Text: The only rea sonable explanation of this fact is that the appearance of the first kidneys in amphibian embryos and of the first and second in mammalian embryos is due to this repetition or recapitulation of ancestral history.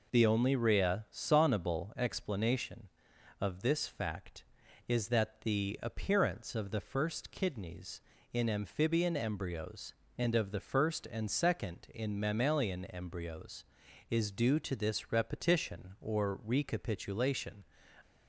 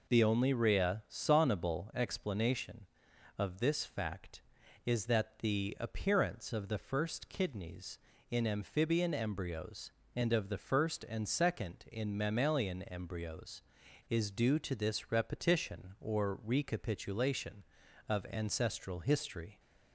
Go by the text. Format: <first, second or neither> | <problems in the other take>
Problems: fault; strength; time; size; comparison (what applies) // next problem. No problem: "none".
second | stops before "of ancestral history"; at 18.0 s